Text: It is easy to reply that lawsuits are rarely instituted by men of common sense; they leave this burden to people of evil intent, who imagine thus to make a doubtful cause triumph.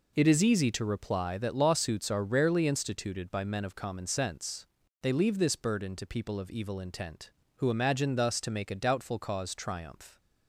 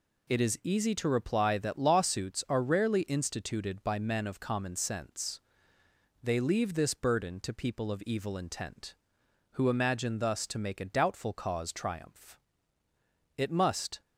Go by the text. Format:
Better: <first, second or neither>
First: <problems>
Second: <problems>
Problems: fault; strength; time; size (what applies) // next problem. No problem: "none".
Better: first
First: none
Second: goes on to say "It must"; noticeable; from 13.3 s on; 0.64 s long